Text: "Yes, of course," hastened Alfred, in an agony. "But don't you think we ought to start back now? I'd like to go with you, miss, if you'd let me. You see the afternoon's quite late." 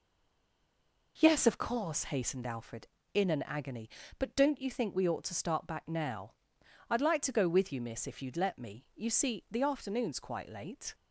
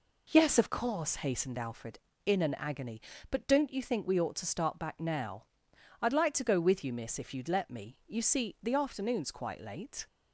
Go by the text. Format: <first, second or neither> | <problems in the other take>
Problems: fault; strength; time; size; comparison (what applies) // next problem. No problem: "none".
second | stays silent before the first word; until 1.1 s; 1.1 s long